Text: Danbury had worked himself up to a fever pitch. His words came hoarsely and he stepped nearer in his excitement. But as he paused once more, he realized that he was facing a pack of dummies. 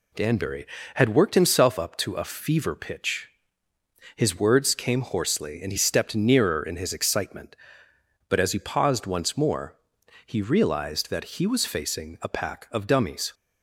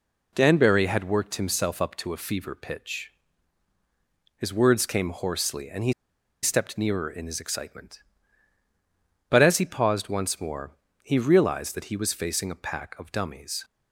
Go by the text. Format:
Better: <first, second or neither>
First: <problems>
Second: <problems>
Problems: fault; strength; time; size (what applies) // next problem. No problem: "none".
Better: first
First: none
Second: pauses between "he" and "stepped"; noticeable; at 5.9 s; 0.49 s long